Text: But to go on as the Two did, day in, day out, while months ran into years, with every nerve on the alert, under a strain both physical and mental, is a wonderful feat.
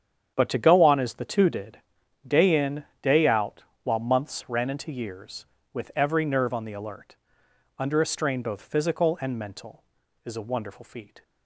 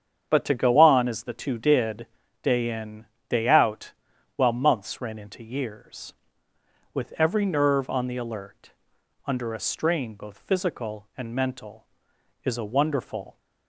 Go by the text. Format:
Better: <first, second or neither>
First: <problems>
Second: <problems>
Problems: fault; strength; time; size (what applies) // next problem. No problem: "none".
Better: first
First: starts louder than the rest; strong; until 1.3 s; 8.5 dB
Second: starts louder than the rest; strong; until 1.3 s; 8 dB // stops before "feat"; at 13.3 s